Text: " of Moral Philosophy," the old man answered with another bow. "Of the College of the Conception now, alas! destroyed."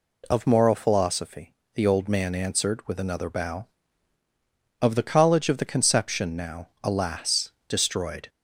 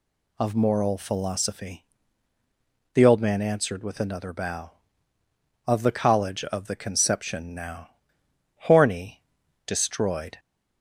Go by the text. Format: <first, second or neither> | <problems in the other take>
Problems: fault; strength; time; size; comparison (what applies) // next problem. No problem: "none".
first | says "horny" for "alas"; at 8.6 s